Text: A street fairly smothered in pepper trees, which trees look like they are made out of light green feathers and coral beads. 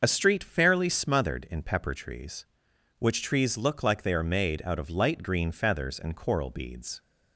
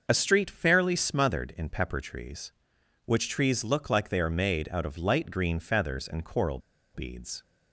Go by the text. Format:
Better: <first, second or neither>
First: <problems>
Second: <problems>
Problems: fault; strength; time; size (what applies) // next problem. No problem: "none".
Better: first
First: starts louder than the rest; noticeable; until 1.0 s; 6 dB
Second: starts louder than the rest; noticeable; until 1.0 s; 6 dB // pauses between "coral" and "beads"; slight; at 6.5 s; 0.35 s long